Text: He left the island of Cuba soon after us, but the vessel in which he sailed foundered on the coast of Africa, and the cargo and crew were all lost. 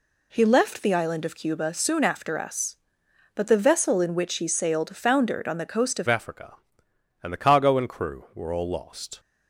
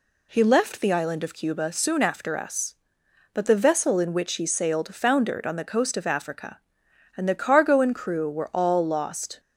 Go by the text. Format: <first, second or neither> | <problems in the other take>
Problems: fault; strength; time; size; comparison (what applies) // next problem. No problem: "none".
second | changes voice at "Africa"; from 6.0 s on; 3.1 s long